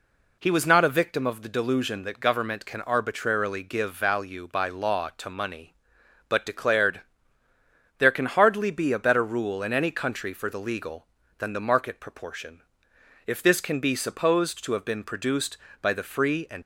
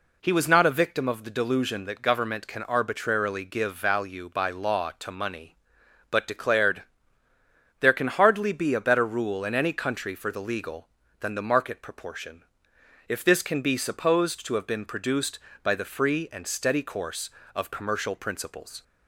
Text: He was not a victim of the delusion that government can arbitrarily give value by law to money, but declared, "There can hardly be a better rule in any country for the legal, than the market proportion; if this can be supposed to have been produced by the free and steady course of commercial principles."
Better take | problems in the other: second | stops before "steady course of commercial principles"; at 16.6 s

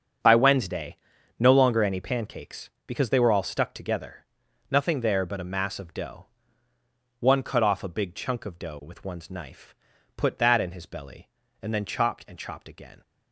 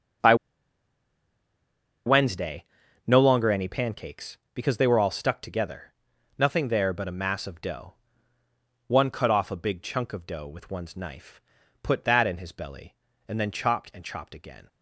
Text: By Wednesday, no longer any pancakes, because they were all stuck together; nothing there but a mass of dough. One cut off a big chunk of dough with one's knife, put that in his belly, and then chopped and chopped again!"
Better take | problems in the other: first | starts louder than the rest; strong; until 3.3 s; 7 dB; strong in the first // pauses between "By" and "Wednesday"; strong; at 0.3 s; 1.7 s long

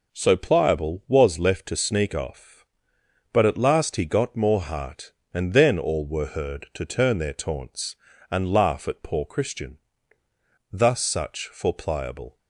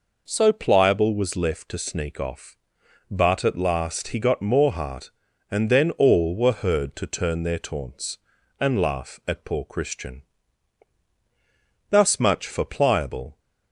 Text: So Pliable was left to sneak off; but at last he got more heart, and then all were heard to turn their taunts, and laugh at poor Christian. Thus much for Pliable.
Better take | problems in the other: second | says "such" for "much"; at 10.9 s

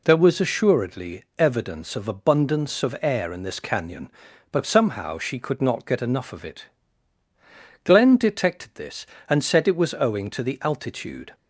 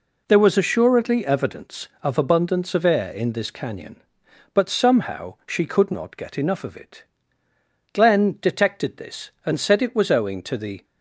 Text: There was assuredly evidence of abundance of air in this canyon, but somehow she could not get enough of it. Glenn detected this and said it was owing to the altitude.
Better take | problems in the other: first | stops before "altitude"; at 10.8 s

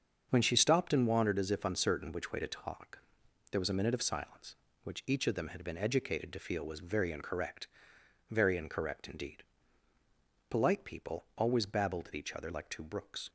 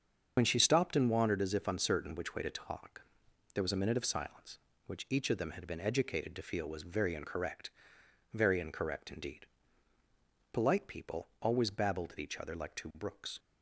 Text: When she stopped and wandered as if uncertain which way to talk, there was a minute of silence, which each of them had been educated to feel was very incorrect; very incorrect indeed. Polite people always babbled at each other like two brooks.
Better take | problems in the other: first | loses the start of "When"; at 0.3 s; 45 ms // starts louder than the rest; until 1.3 s; 7 dB; also in the first

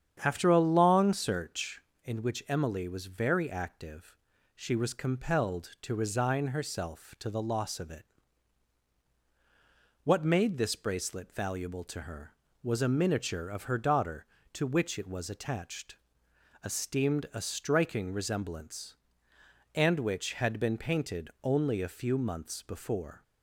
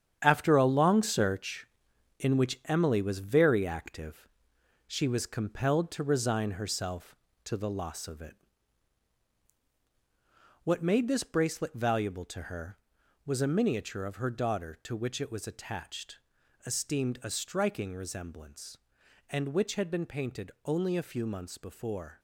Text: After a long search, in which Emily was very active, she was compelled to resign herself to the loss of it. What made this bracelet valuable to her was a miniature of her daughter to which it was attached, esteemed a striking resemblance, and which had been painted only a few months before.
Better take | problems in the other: first | gets quieter; strong; throughout; 8.5 dB // starts louder than the rest; strong; until 1.2 s; 8.5 dB; strong in the first

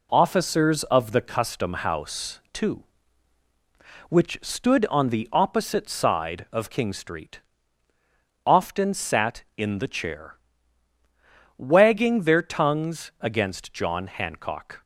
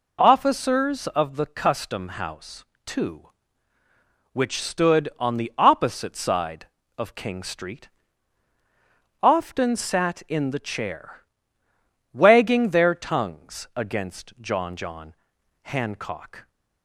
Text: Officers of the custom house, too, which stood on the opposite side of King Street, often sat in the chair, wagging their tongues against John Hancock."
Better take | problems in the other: first | says "John" twice; at 14.7 s

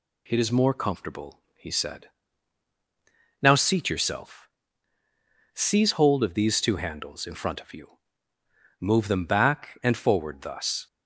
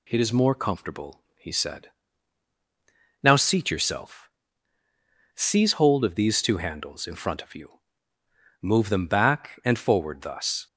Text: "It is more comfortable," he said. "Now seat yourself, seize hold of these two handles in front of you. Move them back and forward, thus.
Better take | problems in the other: neither | none

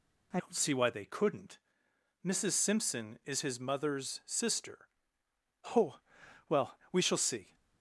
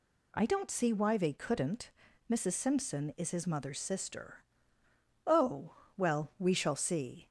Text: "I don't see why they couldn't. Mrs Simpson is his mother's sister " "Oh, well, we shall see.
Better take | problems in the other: second | changes voice at "don't"; from 0.3 s on; 7.2 s long

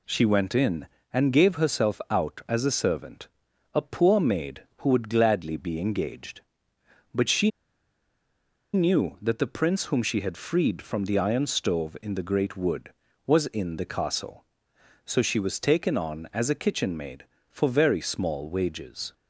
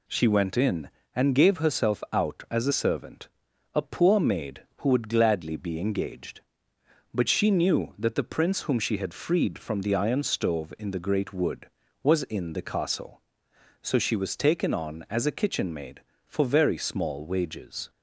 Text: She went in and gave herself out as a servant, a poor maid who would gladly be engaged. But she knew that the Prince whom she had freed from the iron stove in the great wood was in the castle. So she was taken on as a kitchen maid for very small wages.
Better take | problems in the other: second | pauses between "she" and "knew"; at 7.4 s; 1.2 s long

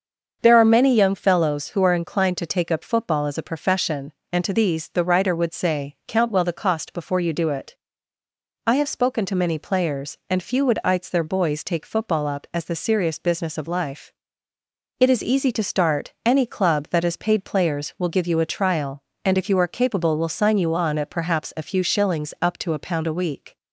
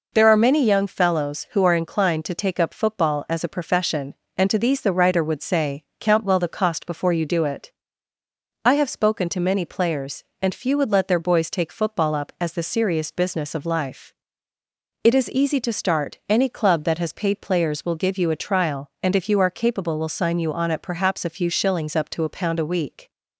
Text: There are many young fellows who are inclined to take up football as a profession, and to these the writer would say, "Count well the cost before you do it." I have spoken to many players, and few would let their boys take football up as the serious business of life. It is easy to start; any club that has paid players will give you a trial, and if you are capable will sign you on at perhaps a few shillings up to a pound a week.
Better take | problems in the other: second | starts louder than the rest; until 1.4 s; 6.5 dB // says "ites" for "let"; at 10.8 s

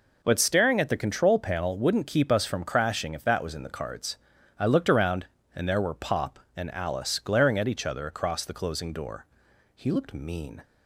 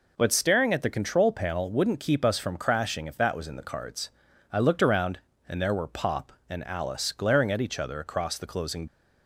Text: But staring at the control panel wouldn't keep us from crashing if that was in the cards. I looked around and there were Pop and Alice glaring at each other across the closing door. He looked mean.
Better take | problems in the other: first | stops before "door He looked mean"; at 8.8 s

